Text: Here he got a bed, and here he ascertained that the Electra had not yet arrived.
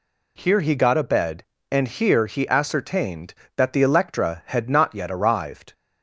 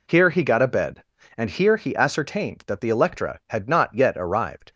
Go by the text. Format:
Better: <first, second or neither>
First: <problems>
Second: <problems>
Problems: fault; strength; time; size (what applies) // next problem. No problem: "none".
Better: first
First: none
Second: gets quieter; strong; throughout; 10.5 dB